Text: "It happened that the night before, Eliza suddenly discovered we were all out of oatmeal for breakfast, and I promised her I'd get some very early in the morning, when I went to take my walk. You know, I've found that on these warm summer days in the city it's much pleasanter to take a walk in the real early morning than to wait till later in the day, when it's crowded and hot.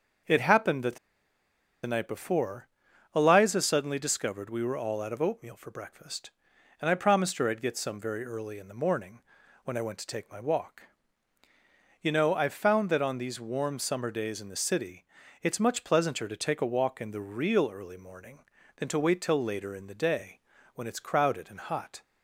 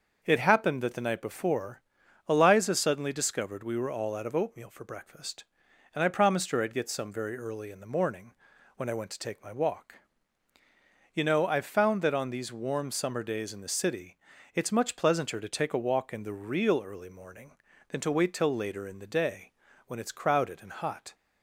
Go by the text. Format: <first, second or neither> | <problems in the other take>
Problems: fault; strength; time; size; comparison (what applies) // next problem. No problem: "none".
second | starts louder than the rest; until 2.1 s; 6.5 dB; also in the second // pauses between "the" and "night"; noticeable; at 0.9 s; 0.87 s long // pauses between "city" and "it's"; slight; at 15.0 s; 0.36 s long; slight in the second